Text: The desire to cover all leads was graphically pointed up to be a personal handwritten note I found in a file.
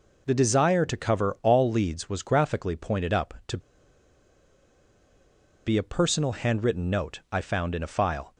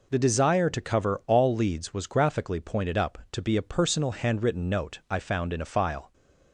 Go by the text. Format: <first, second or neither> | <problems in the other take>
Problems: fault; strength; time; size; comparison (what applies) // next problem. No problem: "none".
second | pauses between "to" and "be"; strong; at 3.5 s; 2.0 s long